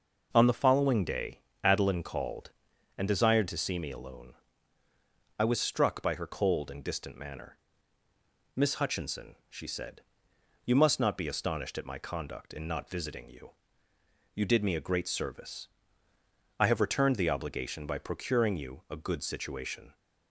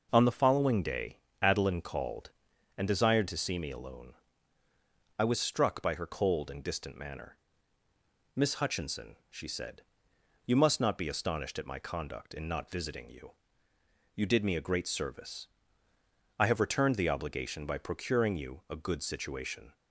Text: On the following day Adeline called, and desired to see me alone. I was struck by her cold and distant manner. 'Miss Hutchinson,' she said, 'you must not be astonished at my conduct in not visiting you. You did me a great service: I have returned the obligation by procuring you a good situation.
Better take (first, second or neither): neither